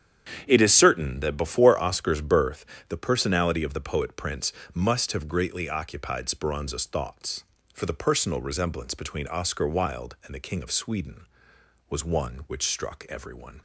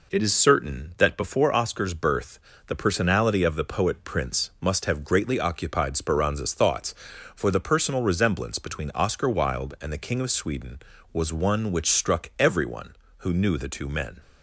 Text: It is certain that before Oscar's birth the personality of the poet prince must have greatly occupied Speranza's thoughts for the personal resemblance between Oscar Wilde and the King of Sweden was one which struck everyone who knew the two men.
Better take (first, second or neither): second